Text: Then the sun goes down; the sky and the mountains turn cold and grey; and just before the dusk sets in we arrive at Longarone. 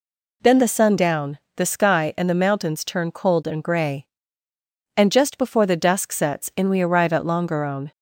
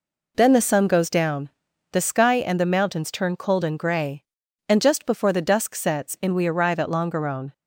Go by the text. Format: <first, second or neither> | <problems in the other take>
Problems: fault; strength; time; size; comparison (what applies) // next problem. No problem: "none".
second | skips "goes"; at 0.9 s